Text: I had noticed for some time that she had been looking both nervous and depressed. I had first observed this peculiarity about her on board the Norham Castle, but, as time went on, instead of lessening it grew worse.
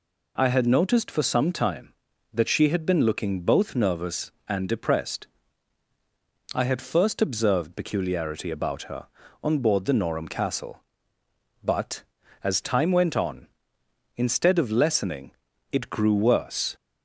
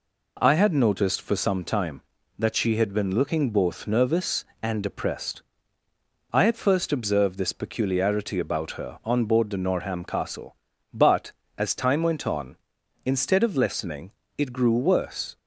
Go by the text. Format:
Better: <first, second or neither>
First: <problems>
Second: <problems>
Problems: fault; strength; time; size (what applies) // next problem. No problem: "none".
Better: second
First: skips "this"; at 7.7 s // pauses between "lessening" and "it"; at 15.3 s; 0.40 s long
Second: pauses between "lessening" and "it"; slight; at 14.1 s; 0.26 s long